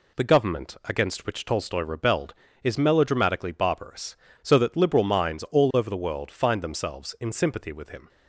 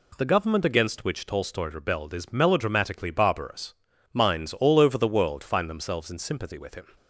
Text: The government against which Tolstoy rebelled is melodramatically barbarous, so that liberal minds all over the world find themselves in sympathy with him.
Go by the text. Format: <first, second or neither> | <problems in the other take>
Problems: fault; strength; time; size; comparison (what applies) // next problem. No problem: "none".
first | skips "so that liberal"; at 3.9 s